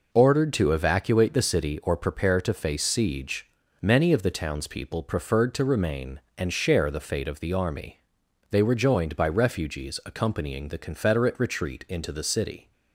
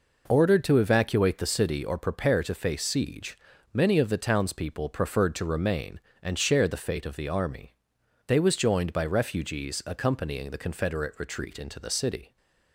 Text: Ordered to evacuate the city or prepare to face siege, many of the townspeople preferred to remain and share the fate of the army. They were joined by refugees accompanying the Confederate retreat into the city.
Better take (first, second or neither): first